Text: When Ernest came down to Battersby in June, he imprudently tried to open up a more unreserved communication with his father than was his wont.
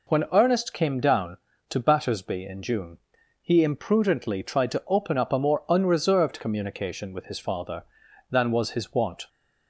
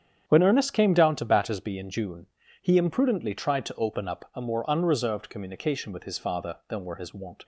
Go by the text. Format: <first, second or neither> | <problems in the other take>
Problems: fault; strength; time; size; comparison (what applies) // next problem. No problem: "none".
first | starts louder than the rest; strong; until 1.2 s; 8.5 dB // says "were" for "was"; at 6.8 s